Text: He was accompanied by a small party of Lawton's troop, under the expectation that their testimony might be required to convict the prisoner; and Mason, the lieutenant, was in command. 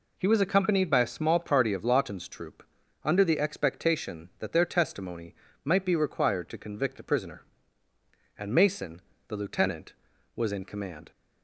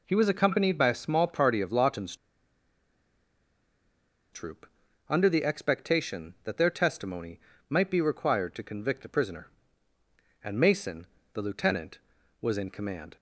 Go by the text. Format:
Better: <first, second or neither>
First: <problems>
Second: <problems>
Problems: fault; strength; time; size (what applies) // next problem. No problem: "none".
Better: first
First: pauses between "testimony" and "might"; slight; at 5.3 s; 0.30 s long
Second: pauses between "Lawton's" and "troop"; strong; at 2.1 s; 2.1 s long // pauses between "testimony" and "might"; slight; at 7.4 s; 0.30 s long